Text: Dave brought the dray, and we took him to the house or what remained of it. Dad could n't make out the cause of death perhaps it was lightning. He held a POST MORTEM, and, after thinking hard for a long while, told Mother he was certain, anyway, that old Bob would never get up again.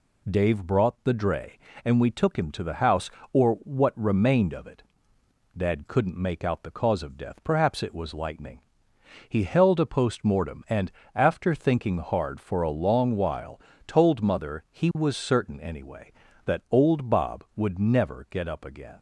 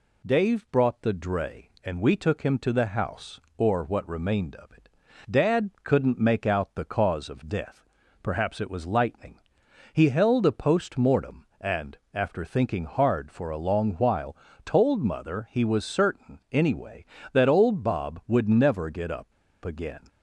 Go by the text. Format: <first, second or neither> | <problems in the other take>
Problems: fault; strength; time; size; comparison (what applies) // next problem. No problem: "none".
first | pauses between "death" and "perhaps"; slight; at 7.8 s; 0.36 s long // pauses between "up" and "again"; slight; at 19.3 s; 0.32 s long